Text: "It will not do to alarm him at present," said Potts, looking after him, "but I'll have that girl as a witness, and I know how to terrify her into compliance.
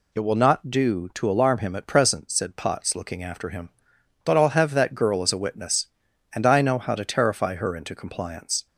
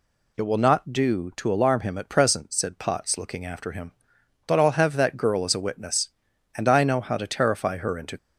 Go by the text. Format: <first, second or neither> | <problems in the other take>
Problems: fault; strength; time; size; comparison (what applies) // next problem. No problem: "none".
first | stops before "compliance"; at 8.1 s